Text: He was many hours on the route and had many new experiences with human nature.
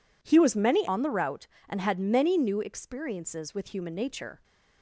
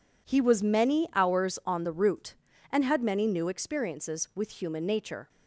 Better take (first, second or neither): second